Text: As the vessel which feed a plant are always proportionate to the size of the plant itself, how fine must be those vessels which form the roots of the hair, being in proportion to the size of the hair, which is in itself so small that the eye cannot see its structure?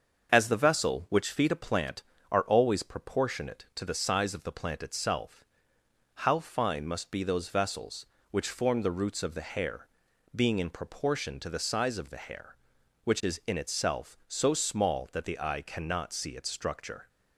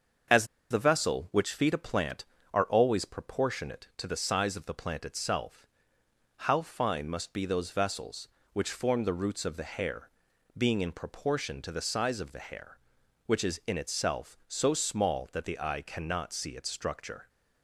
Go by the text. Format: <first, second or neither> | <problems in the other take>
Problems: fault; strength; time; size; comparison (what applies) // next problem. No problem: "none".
first | starts louder than the rest; until 1.5 s; 6.5 dB; also in the first // pauses between "As" and "the"; slight; at 0.4 s; 0.25 s long